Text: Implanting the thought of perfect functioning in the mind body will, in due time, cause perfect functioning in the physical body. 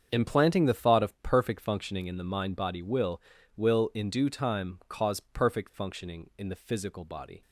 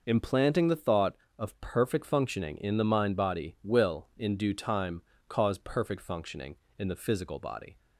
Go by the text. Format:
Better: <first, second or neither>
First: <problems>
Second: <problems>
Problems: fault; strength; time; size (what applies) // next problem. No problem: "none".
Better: second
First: starts louder than the rest; strong; until 1.1 s; 7.5 dB // says "will" twice; at 3.5 s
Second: none